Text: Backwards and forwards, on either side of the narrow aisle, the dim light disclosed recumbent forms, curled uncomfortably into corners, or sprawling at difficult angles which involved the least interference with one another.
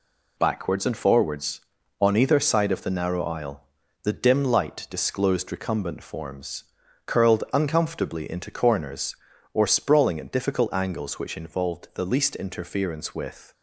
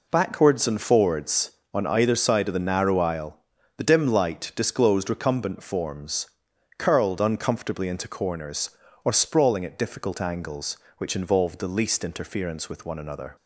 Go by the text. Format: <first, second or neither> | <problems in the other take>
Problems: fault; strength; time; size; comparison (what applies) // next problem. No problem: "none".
second | stops before "one another"; at 13.5 s